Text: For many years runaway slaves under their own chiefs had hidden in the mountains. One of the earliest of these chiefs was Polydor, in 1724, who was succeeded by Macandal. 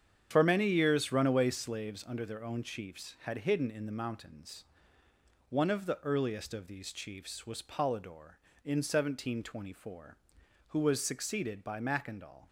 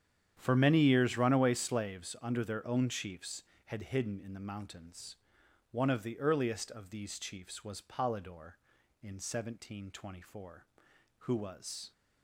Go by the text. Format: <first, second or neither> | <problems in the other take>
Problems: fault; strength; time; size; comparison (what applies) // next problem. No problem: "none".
first | starts louder than the rest; strong; until 1.3 s; 9 dB; strong in the first // stops before "succeeded by Macandal"; at 11.9 s